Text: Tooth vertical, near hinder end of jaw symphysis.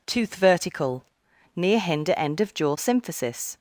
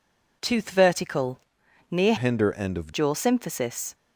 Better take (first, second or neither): first